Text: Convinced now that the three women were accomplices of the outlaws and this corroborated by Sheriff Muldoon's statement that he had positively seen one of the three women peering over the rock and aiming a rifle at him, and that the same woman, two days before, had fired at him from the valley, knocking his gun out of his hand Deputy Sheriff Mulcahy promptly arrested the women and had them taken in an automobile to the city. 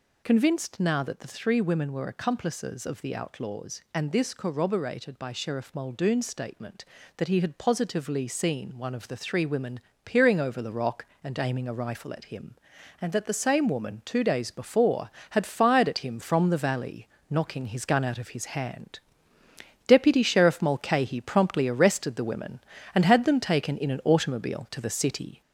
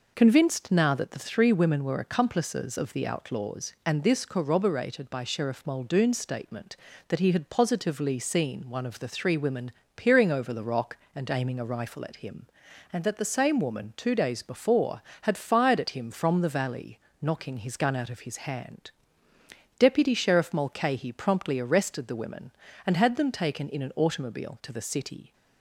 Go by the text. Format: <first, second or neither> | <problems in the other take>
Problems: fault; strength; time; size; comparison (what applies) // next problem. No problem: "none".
second | gets louder; noticeable; throughout; 4 dB // pauses between "women" and "peering"; slight; at 9.7 s; 0.26 s long; slight in the second // pauses between "hand" and "Deputy"; noticeable; at 18.9 s; 0.88 s long; noticeable in the second